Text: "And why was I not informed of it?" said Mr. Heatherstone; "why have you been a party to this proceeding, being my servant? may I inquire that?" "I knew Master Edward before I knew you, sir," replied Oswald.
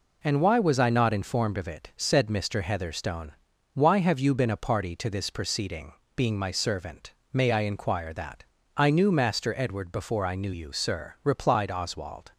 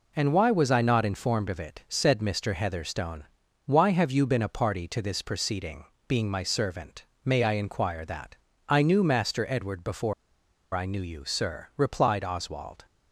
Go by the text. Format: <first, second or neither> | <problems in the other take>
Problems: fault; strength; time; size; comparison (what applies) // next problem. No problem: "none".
first | pauses between "before" and "I"; noticeable; at 10.1 s; 0.60 s long